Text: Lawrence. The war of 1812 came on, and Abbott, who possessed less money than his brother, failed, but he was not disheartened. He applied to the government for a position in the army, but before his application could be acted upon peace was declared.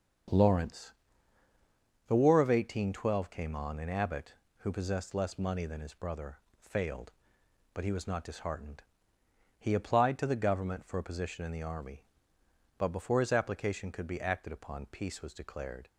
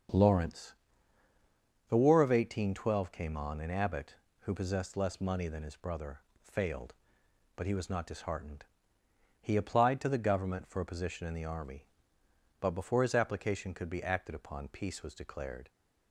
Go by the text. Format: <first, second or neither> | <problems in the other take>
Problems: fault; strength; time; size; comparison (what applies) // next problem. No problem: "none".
neither | starts louder than the rest; the same in both